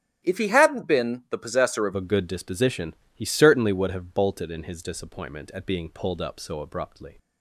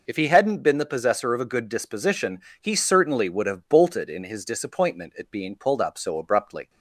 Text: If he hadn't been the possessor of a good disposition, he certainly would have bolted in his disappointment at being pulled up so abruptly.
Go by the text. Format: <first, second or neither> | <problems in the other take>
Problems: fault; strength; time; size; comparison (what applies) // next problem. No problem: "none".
second | starts louder than the rest; strong; until 1.2 s; 10 dB // changes voice at "a"; from 1.9 s on; 5.2 s long